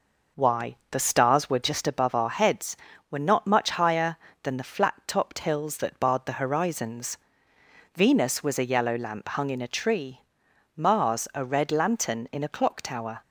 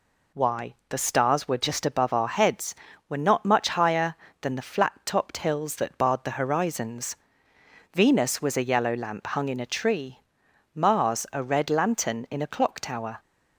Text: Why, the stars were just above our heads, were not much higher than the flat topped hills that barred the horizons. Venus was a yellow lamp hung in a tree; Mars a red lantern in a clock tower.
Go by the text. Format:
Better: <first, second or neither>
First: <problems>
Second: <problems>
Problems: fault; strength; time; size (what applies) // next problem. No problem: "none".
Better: second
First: starts louder than the rest; noticeable; until 1.7 s; 5 dB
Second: none